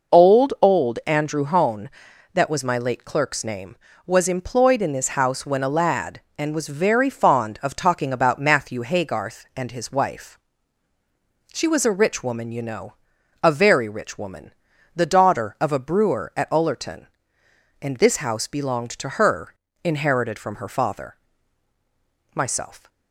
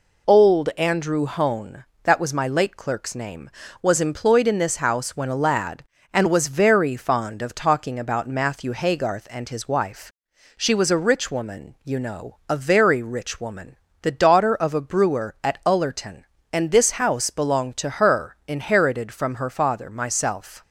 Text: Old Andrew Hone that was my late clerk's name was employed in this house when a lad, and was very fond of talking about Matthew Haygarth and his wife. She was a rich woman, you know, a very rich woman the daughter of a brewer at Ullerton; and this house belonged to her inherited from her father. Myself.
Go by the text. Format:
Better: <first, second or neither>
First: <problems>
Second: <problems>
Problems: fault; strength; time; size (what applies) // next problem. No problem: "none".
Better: second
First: says "Old" twice; at 0.6 s // pauses between "woman" and "the"; at 14.5 s; 0.42 s long // pauses between "her" and "inherited"; slight; at 19.5 s; 0.28 s long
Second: pauses between "woman" and "the"; slight; at 13.7 s; 0.26 s long